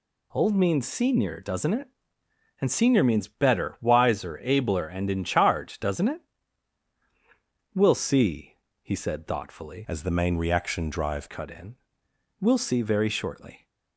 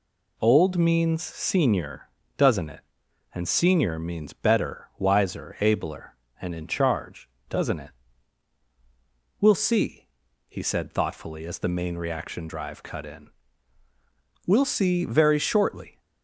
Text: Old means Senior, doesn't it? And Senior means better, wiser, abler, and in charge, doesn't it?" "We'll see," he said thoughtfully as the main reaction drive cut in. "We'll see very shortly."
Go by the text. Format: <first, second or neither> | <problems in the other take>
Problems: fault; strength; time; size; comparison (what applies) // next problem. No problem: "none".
second | changes voice from "as" to "drive"; from 9.8 to 11.2 s; 1.4 s long